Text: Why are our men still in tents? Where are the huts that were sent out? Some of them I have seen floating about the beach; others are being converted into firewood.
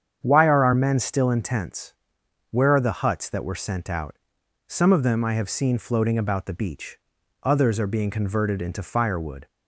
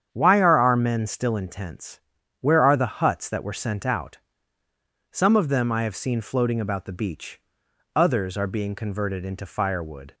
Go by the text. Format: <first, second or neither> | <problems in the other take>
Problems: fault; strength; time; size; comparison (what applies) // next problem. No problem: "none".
neither | starts louder than the rest; strong; the same in both